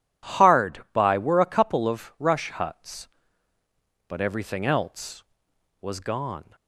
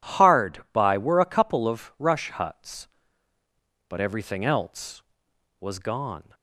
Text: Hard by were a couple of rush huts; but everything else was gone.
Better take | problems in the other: neither | none

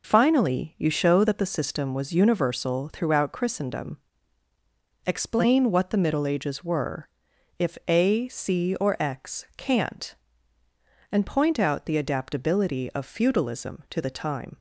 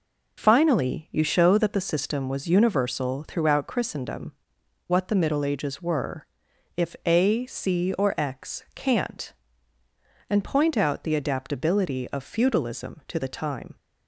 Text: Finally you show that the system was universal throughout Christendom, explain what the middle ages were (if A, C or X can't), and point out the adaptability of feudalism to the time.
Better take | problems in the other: first | skips "explain"; at 4.6 s

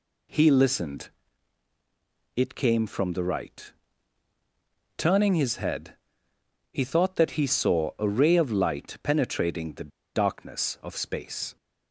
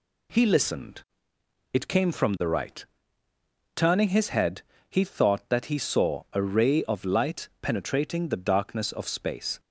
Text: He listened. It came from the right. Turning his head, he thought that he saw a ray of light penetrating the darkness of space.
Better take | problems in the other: second | pauses between "the" and "darkness"; slight; at 9.8 s; 0.25 s long

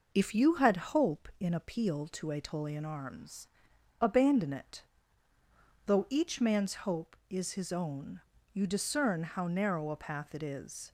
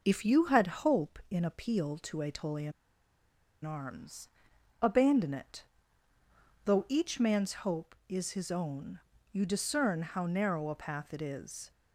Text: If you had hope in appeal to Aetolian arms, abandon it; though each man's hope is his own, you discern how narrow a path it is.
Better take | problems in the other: first | pauses between "Aetolian" and "arms"; noticeable; at 2.7 s; 0.92 s long

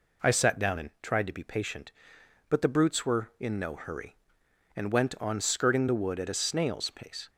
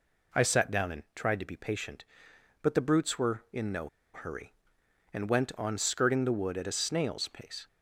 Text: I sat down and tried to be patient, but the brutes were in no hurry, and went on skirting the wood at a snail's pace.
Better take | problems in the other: first | pauses between "no" and "hurry"; slight; at 3.8 s; 0.25 s long

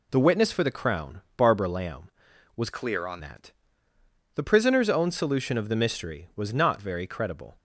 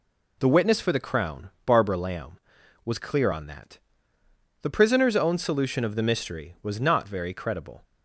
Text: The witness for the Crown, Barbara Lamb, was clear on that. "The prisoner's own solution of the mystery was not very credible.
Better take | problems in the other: second | changes voice from "clear" to "on"; from 2.7 to 3.1 s; 0.4 s long

